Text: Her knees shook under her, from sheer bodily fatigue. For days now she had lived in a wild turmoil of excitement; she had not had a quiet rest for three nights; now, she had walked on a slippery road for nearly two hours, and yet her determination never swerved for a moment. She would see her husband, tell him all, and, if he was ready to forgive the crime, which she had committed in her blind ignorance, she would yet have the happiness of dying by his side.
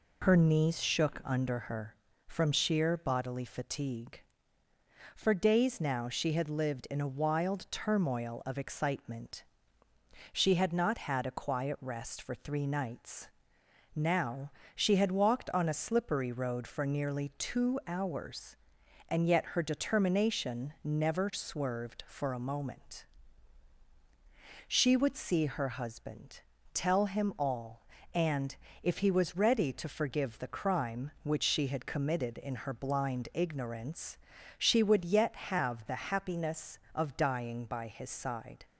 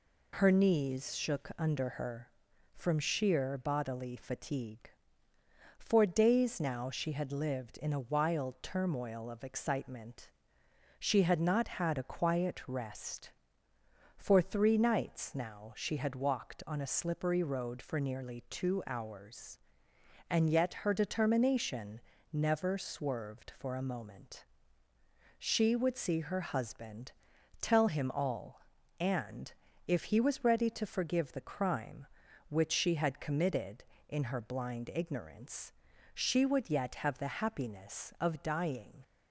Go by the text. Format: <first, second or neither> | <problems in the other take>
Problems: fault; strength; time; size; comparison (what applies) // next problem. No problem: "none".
first | pauses between "determination" and "never"; slight; at 22.0 s; 0.32 s long // stops before "by his side"; at 39.0 s